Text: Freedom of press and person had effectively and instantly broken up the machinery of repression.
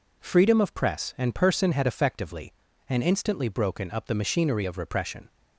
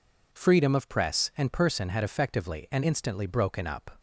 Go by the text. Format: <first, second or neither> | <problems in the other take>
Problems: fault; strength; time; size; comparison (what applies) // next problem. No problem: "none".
first | stops before "the machinery of repression"; at 3.9 s